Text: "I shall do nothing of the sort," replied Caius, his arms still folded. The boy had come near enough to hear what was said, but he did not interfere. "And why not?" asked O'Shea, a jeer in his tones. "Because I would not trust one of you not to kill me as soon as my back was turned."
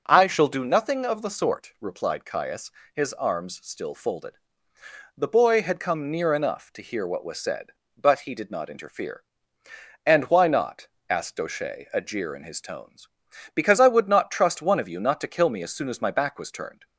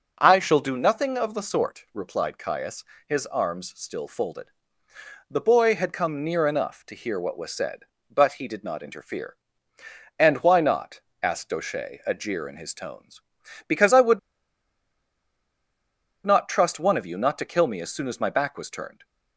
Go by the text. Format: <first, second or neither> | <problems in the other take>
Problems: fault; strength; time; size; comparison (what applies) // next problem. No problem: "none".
first | pauses between "would" and "not"; strong; at 14.1 s; 2.0 s long